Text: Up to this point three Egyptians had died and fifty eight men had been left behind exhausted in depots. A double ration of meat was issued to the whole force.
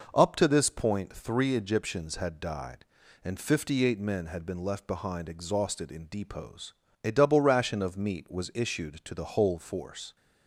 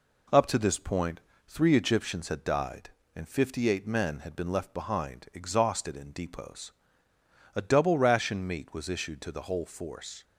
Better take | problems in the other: first | pauses between "point" and "three"; slight; at 1.2 s; 0.26 s long // skips "of"; at 8.4 s

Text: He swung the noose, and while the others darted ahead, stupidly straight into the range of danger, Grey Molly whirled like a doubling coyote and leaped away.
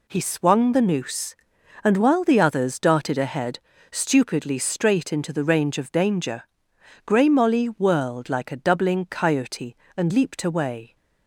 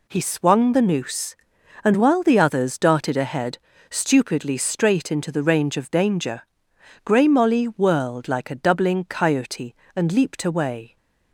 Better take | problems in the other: neither | none

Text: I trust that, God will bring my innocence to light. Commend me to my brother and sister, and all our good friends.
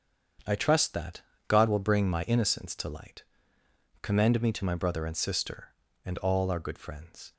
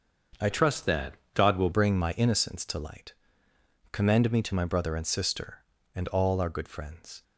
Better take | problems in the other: first | starts louder than the rest; until 1.5 s; 6.5 dB; strong in the first // changes voice from "trust" to "will"; from 0.4 to 1.7 s; 1.3 s long

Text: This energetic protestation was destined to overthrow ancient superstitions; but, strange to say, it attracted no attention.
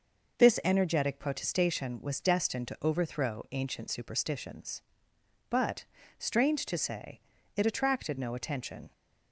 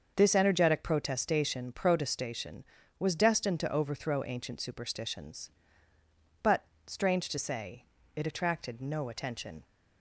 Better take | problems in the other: first | starts louder than the rest; until 1.1 s; 6.5 dB // says "protestation" twice; at 1.7 s

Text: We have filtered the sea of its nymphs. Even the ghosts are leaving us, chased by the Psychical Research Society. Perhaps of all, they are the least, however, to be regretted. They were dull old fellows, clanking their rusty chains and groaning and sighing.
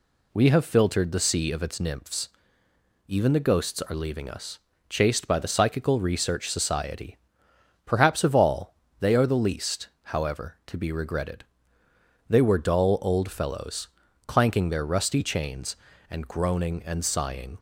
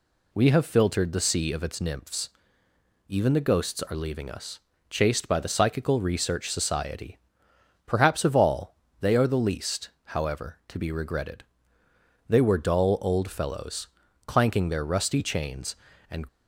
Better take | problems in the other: first | stops before "groaning and sighing"; at 16.2 s

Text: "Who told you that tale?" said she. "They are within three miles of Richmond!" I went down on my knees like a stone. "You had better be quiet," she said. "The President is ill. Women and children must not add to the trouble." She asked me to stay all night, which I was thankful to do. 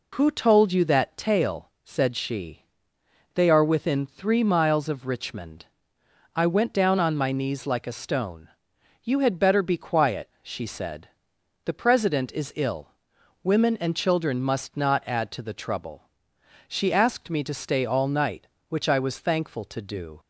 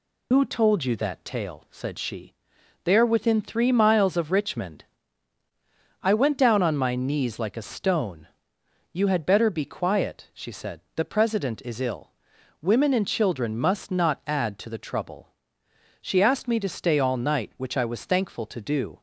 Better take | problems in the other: first | loses the start of "Who"; at 0.3 s; 75 ms

